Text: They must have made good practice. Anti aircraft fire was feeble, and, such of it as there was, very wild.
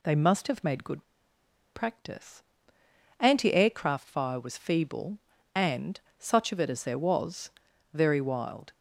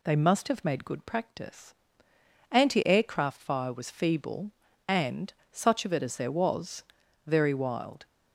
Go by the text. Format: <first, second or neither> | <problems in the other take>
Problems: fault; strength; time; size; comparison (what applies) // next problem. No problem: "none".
second | pauses between "good" and "practice"; noticeable; at 1.0 s; 0.69 s long